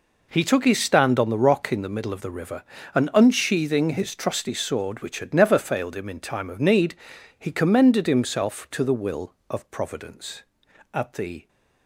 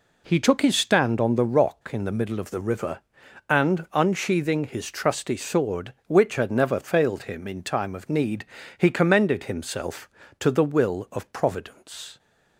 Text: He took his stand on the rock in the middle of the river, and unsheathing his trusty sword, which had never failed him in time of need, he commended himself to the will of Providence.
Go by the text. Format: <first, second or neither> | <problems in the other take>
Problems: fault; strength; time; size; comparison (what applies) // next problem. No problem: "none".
second | goes on to say "At the"; from 10.9 s on; 0.56 s long